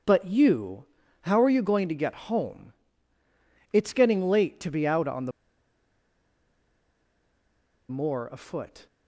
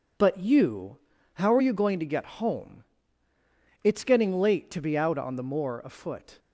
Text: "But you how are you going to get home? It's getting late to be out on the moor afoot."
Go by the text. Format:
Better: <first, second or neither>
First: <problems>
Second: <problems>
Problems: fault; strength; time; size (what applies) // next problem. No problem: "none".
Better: second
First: pauses between "you" and "how"; at 0.8 s; 0.38 s long // pauses between "the" and "moor"; strong; at 5.3 s; 2.5 s long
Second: pauses between "you" and "how"; at 0.9 s; 0.38 s long